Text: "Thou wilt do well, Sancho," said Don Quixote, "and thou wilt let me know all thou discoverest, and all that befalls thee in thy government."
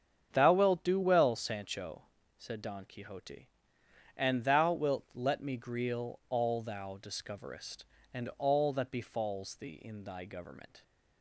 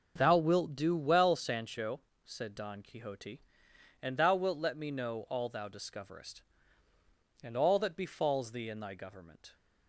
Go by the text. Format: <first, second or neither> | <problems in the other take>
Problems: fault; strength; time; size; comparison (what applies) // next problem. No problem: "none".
second | starts louder than the rest; strong; until 1.3 s; 8 dB // says "greal" for "know"; at 5.5 s